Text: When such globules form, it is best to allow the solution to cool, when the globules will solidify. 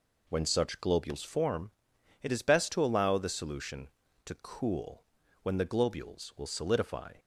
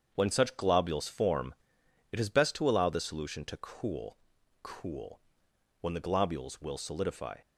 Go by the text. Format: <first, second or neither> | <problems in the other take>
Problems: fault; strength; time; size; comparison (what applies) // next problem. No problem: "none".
first | starts louder than the rest; strong; until 1.1 s; 7 dB // says "cool" twice; at 4.6 s